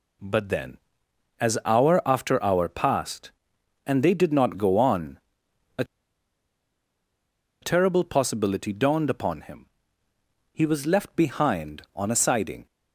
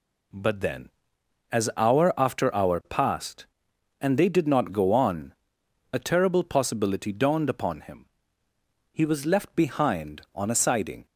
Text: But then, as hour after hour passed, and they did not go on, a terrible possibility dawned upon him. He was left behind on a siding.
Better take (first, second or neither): second